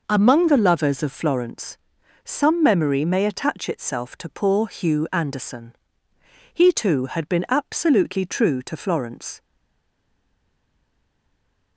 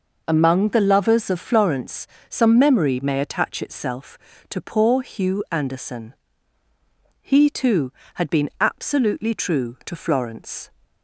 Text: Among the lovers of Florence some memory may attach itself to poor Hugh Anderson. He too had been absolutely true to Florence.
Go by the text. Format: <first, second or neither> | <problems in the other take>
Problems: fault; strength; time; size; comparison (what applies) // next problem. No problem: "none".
second | pauses between "Florence" and "some"; noticeable; at 1.7 s; 0.46 s long; slight in the second // stays silent after the last word; from 9.4 s on; 2.3 s long